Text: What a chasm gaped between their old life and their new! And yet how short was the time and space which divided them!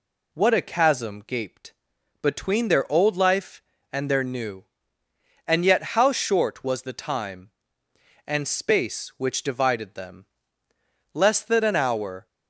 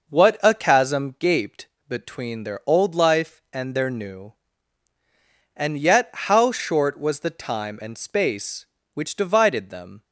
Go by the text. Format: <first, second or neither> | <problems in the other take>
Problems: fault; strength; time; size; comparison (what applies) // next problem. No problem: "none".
second | pauses between "gaped" and "between"; noticeable; at 1.7 s; 0.48 s long; slight in the second // goes on to say "Less than an hour"; noticeable; from 11.1 s on; 1.1 s long